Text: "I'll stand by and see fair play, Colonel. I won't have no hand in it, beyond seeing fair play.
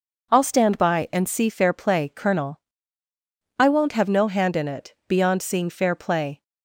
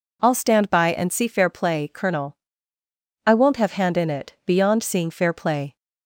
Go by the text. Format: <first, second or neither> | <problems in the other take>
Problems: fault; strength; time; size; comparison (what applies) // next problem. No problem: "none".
first | skips "no"; at 3.7 s